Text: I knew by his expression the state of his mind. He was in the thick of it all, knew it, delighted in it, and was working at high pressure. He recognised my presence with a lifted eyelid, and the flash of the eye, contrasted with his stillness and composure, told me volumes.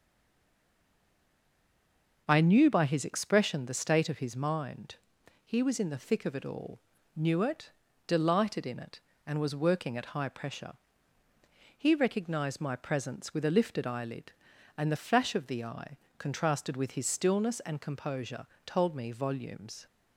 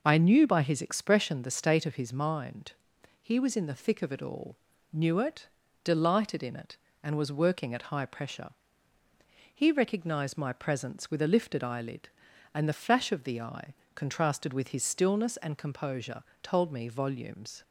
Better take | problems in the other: second | stays silent before the first word; until 2.2 s; 2.2 s long

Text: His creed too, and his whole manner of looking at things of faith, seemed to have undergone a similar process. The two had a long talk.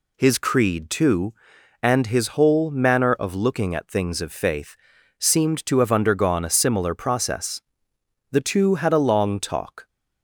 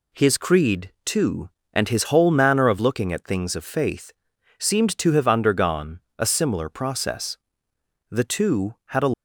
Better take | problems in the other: first | pauses between "undergone" and "a"; slight; at 6.0 s; 0.18 s long // stops before "long talk"; at 9.1 s

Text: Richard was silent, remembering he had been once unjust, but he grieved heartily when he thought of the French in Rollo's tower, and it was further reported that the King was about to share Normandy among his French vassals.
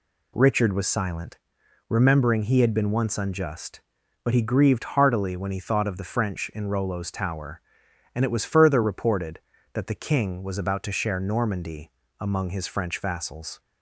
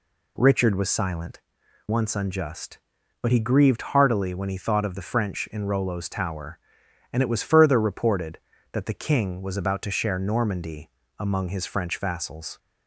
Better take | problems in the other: first | skips "remembering he had been"; at 1.6 s // pauses between "Normandy" and "among"; slight; at 10.8 s; 0.28 s long; slight in the first

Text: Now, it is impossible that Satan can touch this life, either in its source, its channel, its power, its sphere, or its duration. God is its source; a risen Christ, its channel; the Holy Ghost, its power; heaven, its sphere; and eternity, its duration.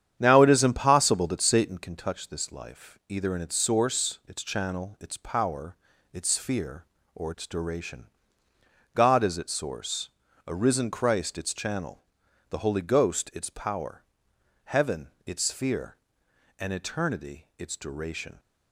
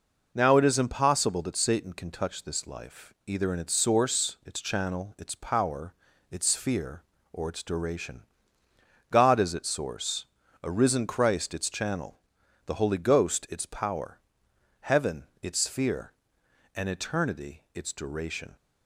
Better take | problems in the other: second | starts louder than the rest; strong; until 1.8 s; 9 dB

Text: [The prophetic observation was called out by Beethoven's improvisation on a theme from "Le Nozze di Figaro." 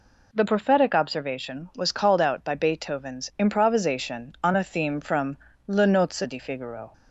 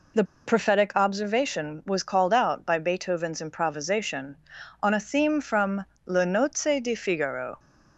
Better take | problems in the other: first | pauses between "The" and "prophetic"; slight; at 0.2 s; 0.23 s long // pauses between "from" and "Le"; slight; at 5.8 s; 0.22 s long; slight in the first

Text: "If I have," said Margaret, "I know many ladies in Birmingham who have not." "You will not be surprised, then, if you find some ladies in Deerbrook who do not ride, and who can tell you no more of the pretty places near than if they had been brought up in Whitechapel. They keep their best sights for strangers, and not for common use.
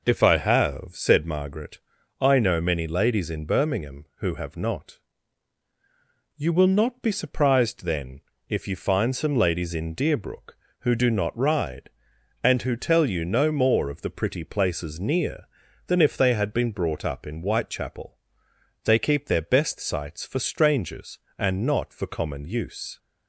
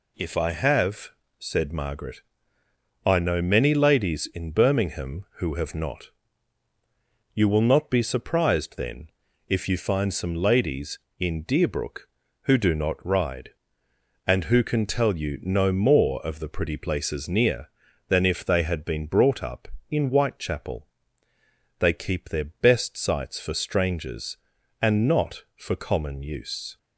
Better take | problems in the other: second | skips "can"; at 12.7 s

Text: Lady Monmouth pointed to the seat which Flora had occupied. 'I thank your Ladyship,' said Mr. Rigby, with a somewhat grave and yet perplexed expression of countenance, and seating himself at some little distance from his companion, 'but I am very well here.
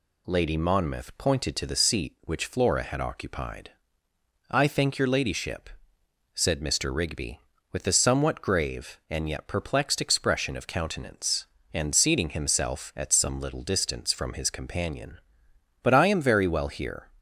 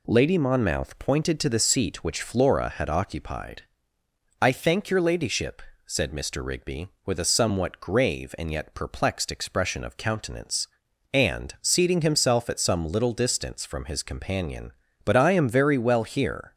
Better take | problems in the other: neither | none

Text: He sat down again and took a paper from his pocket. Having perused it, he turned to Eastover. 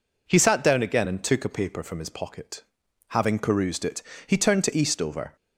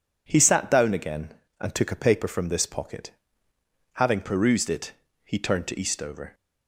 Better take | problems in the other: first | says "this" for "his"; at 2.4 s

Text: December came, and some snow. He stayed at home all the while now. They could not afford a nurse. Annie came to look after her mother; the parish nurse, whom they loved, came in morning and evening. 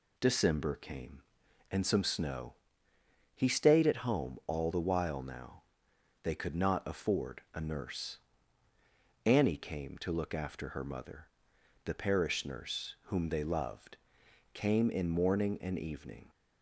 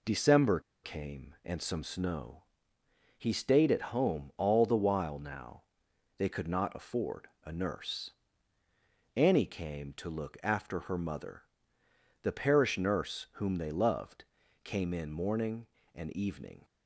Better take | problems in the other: first | pauses between "December" and "came"; slight; at 0.5 s; 0.24 s long // pauses between "afford" and "a"; slight; at 7.2 s; 0.18 s long

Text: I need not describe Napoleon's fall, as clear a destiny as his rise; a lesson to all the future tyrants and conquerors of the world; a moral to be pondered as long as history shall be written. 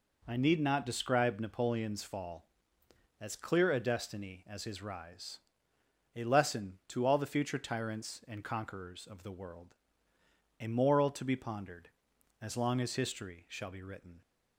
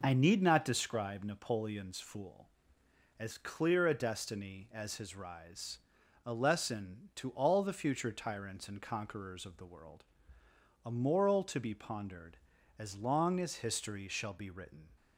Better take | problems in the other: first | says "fool" for "fall"; at 1.9 s

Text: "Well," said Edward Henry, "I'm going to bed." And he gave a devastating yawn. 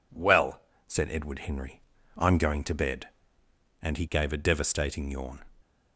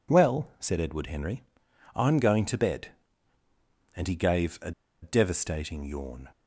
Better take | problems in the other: first | pauses between "a" and "devastating"; slight; at 4.7 s; 0.30 s long

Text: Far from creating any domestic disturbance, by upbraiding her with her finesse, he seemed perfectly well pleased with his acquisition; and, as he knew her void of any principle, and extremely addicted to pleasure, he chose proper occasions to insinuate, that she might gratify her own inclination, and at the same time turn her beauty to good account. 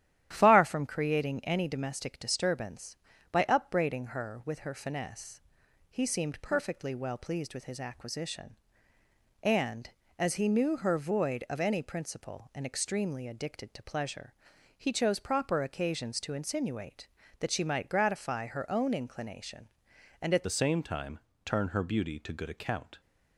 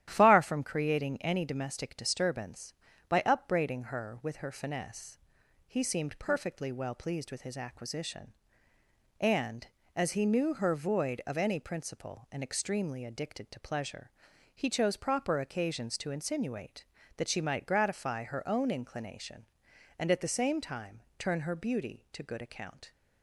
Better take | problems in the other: second | starts louder than the rest; strong; until 1.3 s; 11.5 dB; strong in the second // changes voice at "the"; from 20.4 s on; 2.6 s long // pauses between "time" and "turn"; slight; at 21.1 s; 0.26 s long; slight in the second

